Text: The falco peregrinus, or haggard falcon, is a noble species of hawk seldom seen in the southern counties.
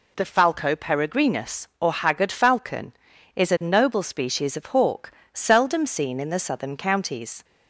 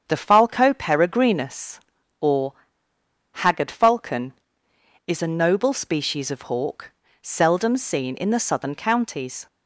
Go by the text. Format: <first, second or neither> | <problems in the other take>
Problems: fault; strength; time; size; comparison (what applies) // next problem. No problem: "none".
first | starts louder than the rest; strong; until 1.0 s; 7.5 dB // pauses between "or" and "haggard"; noticeable; at 2.5 s; 0.80 s long // pauses between "hawk" and "seldom"; slight; at 6.9 s; 0.30 s long; slight in the first